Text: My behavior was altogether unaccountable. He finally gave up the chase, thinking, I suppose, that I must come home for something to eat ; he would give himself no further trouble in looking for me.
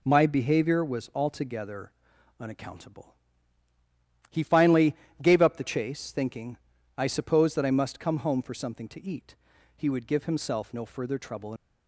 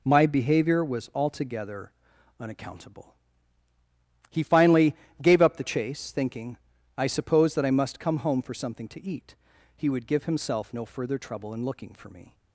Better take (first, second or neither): second